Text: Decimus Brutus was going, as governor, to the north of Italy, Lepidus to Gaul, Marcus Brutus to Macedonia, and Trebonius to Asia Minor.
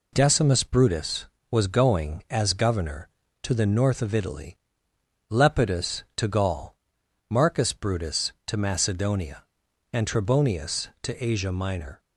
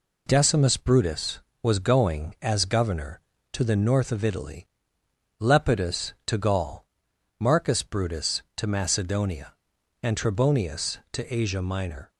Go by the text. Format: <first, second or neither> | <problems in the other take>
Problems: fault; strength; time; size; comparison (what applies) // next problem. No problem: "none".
neither | none